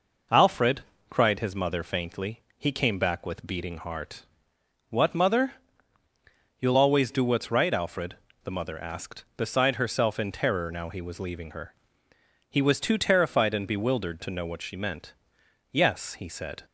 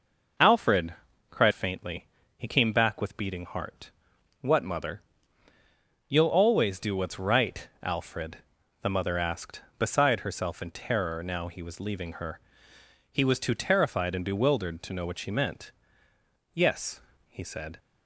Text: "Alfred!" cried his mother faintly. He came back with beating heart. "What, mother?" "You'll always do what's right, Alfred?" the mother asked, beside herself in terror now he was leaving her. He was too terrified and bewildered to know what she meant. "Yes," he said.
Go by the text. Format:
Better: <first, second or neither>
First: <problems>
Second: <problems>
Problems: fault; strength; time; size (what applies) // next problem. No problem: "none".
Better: first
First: none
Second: skips "his mother"; at 1.5 s